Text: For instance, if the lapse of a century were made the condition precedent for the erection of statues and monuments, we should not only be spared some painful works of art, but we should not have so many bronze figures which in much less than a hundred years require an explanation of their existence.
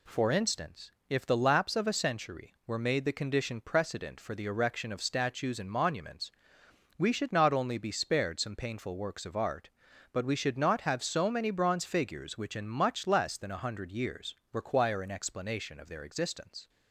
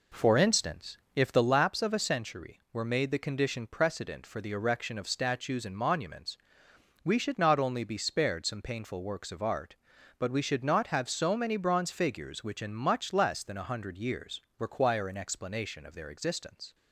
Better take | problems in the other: first | starts louder than the rest; until 1.5 s; 3.5 dB // pauses between "years" and "require"; slight; at 14.4 s; 0.18 s long; slight in the first

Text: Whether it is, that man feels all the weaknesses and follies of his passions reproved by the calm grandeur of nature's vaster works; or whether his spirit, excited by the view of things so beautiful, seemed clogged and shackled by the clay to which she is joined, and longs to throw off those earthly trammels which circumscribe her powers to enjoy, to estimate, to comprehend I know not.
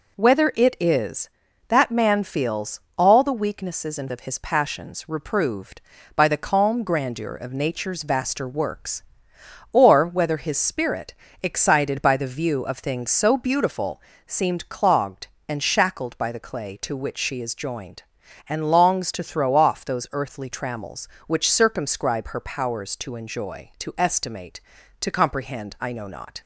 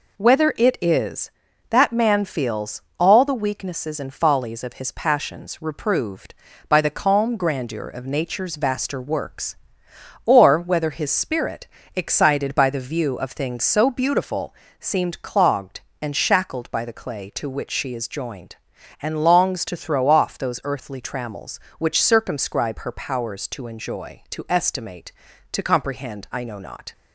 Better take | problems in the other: second | pauses between "feels" and "all"; slight; at 2.8 s; 0.18 s long; slight in the second // skips "follies"; at 4.0 s

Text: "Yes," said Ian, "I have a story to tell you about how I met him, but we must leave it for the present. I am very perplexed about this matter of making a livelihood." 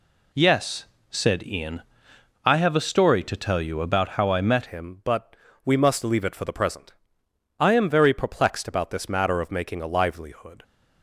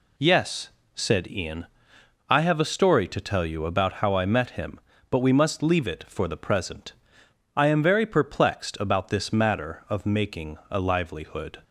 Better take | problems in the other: second | changes voice at "him"; from 4.6 s on; 6.0 s long // pauses between "but" and "we"; slight; at 5.3 s; 0.28 s long

